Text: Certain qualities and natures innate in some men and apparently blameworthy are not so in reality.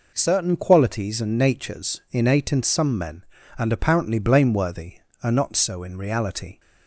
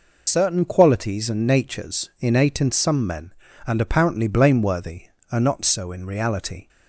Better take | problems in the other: first | loses the start of "Certain"; at 0.2 s; 50 ms

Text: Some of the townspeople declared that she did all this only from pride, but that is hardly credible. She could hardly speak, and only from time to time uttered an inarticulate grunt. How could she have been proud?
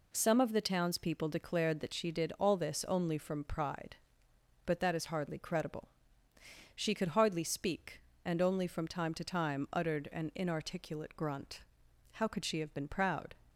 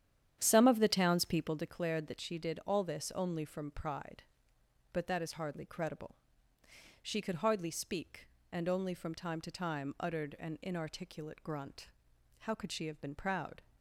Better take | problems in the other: first | starts louder than the rest; strong; until 1.7 s; 9.5 dB

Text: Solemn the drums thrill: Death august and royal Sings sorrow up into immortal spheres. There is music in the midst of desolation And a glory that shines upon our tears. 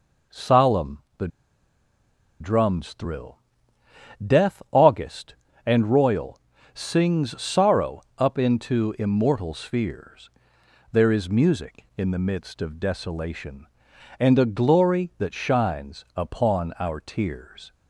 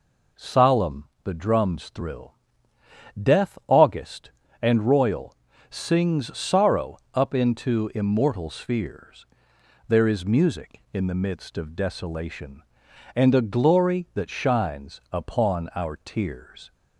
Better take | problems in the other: second | pauses between "the" and "drums"; at 1.2 s; 1.1 s long // pauses between "royal" and "Sings"; slight; at 6.4 s; 0.32 s long; slight in the second // pauses between "sorrow" and "up"; slight; at 8.0 s; 0.16 s long; slight in the second

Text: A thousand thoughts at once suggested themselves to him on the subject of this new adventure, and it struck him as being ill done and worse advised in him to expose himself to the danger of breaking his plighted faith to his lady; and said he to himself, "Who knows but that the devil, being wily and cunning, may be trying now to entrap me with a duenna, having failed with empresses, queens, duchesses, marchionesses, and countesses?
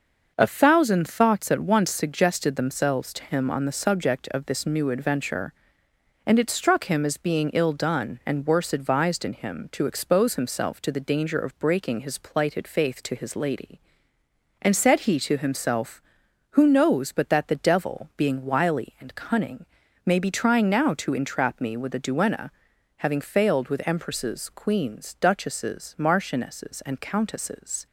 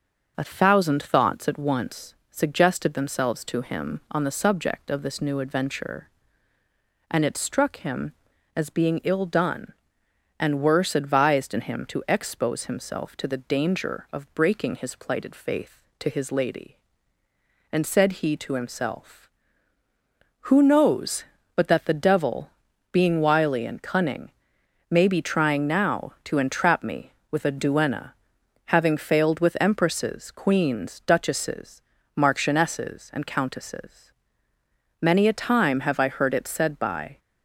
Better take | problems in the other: first | starts louder than the rest; noticeable; until 1.3 s; 6 dB; noticeable in the first // pauses between "once" and "suggested"; slight; at 2.1 s; 0.16 s long // goes on to say "Many a time have I heard it said by"; strong; from 35.0 s on; 2.1 s long

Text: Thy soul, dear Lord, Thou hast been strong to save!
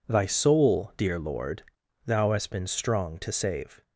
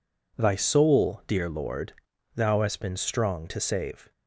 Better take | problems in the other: neither | none

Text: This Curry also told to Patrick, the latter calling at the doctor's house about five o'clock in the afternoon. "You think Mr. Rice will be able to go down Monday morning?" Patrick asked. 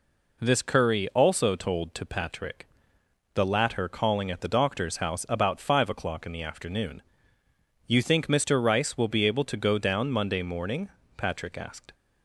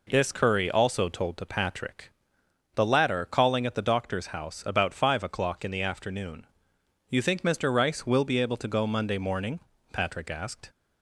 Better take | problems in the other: first | skips "down"; at 8.8 s

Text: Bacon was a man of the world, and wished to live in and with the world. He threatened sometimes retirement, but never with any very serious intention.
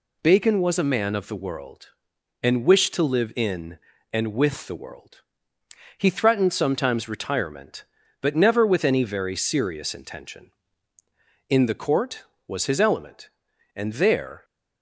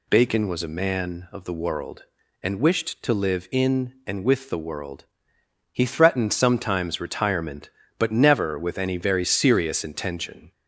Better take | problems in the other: second | goes on to say "In the Court was his element and there"; strong; from 11.4 s on; 2.9 s long

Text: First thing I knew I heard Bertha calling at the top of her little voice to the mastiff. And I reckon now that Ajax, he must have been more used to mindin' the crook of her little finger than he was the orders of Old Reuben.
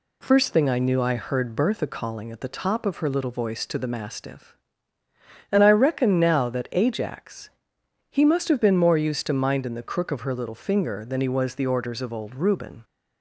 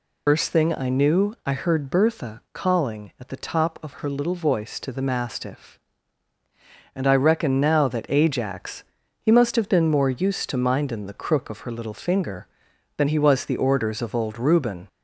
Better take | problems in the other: first | loses the start of "First"; at 0.2 s; 105 ms

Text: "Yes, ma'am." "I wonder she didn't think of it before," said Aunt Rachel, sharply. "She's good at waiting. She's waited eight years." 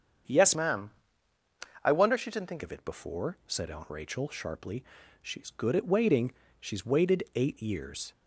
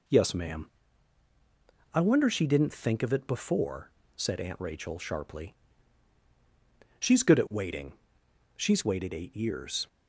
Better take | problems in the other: second | starts louder than the rest; strong; until 2.2 s; 7.5 dB // changes voice from "ma'am" to "think"; from 0.5 to 2.6 s; 2.1 s long

